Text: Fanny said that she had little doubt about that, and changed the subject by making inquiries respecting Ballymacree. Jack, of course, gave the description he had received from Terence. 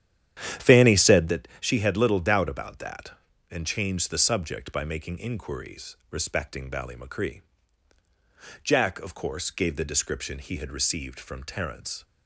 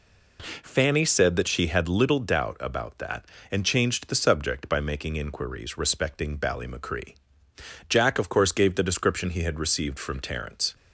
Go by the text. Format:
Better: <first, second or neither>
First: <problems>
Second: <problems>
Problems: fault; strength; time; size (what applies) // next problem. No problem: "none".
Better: second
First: starts louder than the rest; strong; until 1.4 s; 10 dB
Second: none